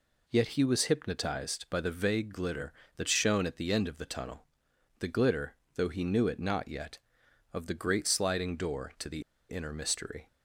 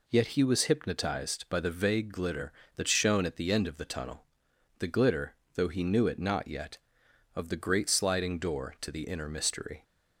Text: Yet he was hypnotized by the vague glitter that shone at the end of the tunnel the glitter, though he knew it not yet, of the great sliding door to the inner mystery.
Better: second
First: pauses between "tunnel" and "the"; noticeable; at 4.4 s; 0.54 s long // pauses between "the" and "inner"; slight; at 9.2 s; 0.28 s long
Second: pauses between "tunnel" and "the"; noticeable; at 4.2 s; 0.54 s long

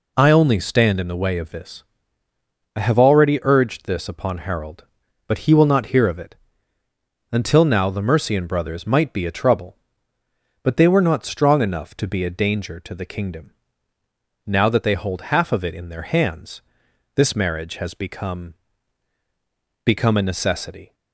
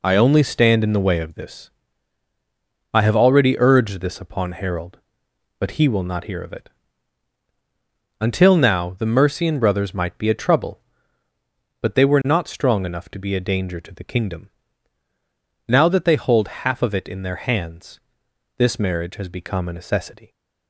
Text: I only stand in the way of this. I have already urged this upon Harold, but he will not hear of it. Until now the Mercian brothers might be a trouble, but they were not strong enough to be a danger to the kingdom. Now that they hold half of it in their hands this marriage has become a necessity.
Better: second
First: pauses between "hands" and "this"; noticeable; at 16.6 s; 0.54 s long // says "become" twice; at 19.8 s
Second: pauses between "hands" and "this"; noticeable; at 17.9 s; 0.60 s long

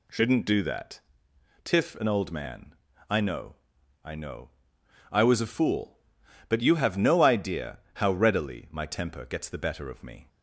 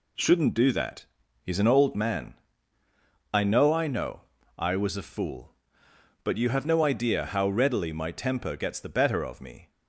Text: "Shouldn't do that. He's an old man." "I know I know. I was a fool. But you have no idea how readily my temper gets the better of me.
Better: second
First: says "Tiff" for "He's"; at 1.6 s // pauses between "know" and "I"; noticeable; at 3.5 s; 0.48 s long // pauses between "idea" and "how"; slight; at 7.7 s; 0.16 s long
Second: none

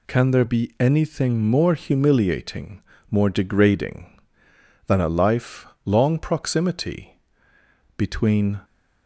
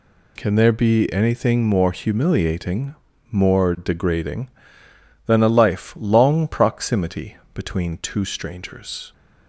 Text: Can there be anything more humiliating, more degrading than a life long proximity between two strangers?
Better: second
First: pauses between "life" and "long"; slight; at 5.6 s; 0.18 s long // pauses between "proximity" and "between"; noticeable; at 7.1 s; 0.78 s long // stops before "two strangers"; at 8.6 s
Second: pauses between "proximity" and "between"; slight; at 7.3 s; 0.18 s long

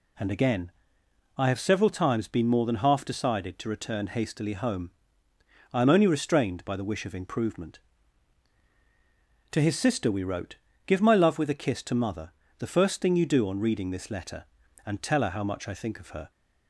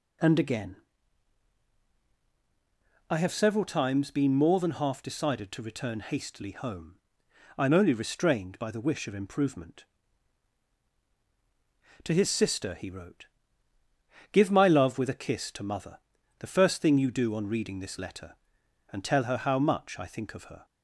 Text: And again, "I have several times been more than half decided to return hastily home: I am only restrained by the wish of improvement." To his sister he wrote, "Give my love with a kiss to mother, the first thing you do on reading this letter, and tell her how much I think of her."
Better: second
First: says "we" for "he"; at 10.1 s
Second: none

